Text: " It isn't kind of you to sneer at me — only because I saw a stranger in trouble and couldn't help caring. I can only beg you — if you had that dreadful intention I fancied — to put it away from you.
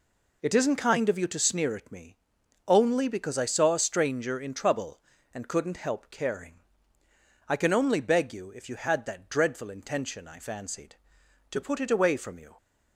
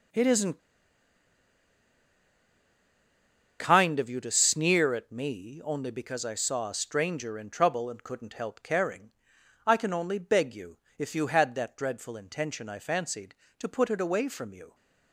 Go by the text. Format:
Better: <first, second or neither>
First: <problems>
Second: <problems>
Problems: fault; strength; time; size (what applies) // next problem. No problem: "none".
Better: first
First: none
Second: pauses between "isn't" and "kind"; strong; at 0.5 s; 2.9 s long